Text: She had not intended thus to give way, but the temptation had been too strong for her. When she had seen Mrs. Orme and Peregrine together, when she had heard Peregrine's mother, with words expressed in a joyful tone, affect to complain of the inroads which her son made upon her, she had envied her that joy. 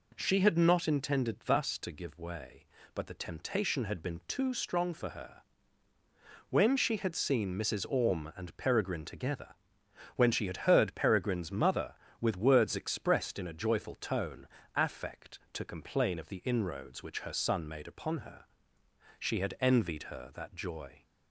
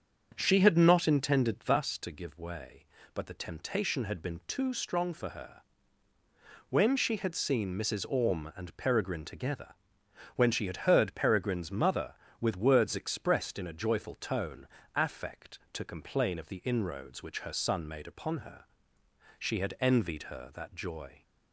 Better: first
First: none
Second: starts louder than the rest; until 1.8 s; 6.5 dB

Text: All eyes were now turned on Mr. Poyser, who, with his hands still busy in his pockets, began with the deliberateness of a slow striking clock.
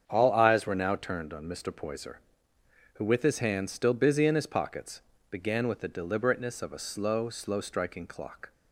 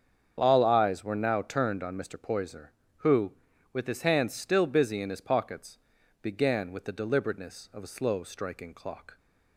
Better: second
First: starts louder than the rest; strong; until 1.0 s; 7.5 dB // says "slow" twice; at 7.3 s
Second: starts louder than the rest; strong; until 1.3 s; 7.5 dB

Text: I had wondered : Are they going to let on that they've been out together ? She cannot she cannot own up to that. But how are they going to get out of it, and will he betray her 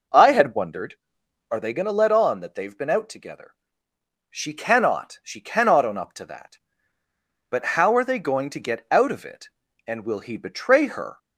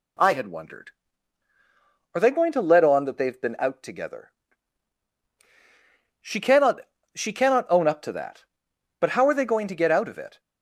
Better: first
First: none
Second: pauses between "cannot" and "she"; slight; at 6.7 s; 0.34 s long // stops before "and will he betray her"; at 10.3 s

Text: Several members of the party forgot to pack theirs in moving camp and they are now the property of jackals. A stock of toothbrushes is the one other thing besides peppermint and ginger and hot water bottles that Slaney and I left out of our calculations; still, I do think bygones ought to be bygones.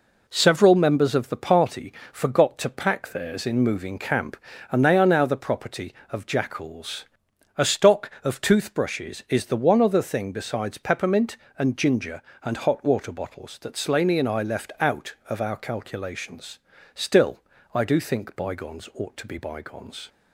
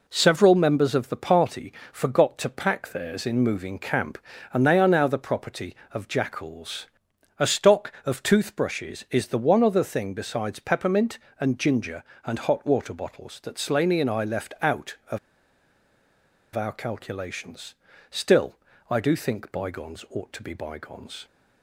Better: first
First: pauses between "party" and "forgot"; slight; at 1.9 s; 0.18 s long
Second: pauses between "party" and "forgot"; slight; at 1.7 s; 0.18 s long // pauses between "of" and "our"; strong; at 15.1 s; 1.3 s long

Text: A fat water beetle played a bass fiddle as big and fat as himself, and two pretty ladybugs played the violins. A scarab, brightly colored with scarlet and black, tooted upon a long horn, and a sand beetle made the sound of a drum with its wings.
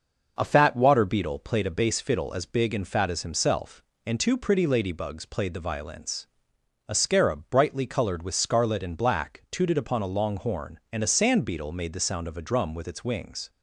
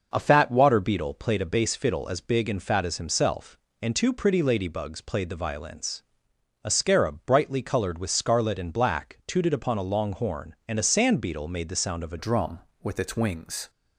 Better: first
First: none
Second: changes voice at "drum"; from 12.1 s on; 1.5 s long

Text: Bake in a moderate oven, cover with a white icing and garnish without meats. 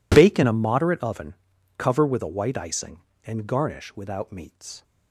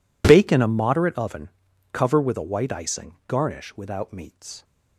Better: first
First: none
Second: skips "and"; at 3.2 s

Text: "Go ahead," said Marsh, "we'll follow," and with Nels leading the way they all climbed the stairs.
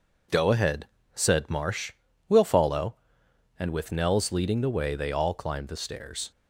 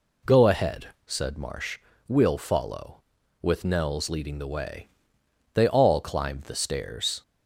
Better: first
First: none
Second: skips "and"; at 3.2 s // pauses between "way" and "they"; noticeable; at 4.8 s; 0.64 s long

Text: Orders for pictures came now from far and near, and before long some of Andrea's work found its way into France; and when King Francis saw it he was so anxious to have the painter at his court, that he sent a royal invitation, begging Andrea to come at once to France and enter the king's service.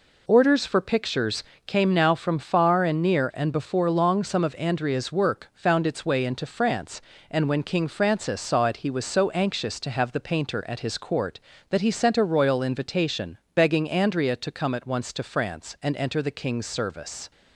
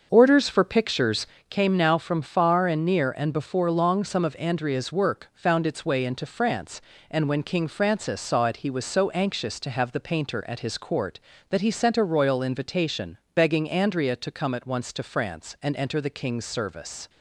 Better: first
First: pauses between "pictures" and "came"; slight; at 1.4 s; 0.24 s long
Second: starts louder than the rest; until 1.3 s; 6.5 dB // pauses between "pictures" and "came"; slight; at 1.2 s; 0.24 s long

